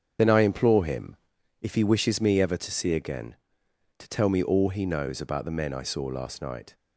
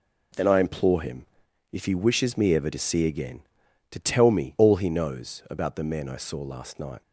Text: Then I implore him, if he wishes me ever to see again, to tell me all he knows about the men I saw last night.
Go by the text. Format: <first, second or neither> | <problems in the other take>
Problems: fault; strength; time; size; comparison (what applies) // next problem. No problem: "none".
second | loses the start of "Then"; at 0.1 s; 40 ms // starts louder than the rest; strong; until 1.6 s; 7.5 dB